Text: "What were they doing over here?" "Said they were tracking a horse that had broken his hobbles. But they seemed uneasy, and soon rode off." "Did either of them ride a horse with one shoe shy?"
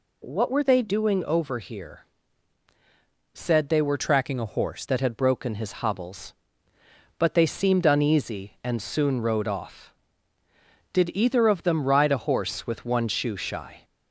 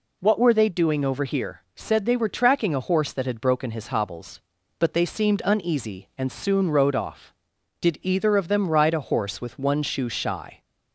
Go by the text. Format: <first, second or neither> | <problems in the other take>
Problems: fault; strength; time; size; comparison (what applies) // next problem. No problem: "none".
second | changes voice from "tracking" to "horse"; from 3.9 to 4.8 s; 0.9 s long